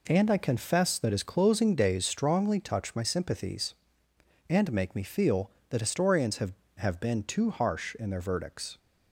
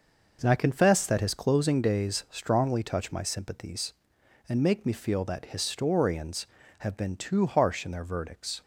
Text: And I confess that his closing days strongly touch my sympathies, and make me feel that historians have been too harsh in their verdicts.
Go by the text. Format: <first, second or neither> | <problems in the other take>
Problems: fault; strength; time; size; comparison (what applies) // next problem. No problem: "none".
second | says "have" twice; at 6.7 s